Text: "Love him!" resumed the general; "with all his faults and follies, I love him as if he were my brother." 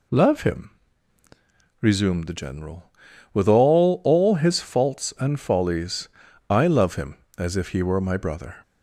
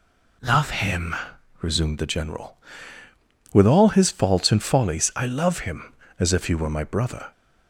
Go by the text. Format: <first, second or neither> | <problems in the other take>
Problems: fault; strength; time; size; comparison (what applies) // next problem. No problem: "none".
second | says "all" twice; at 4.0 s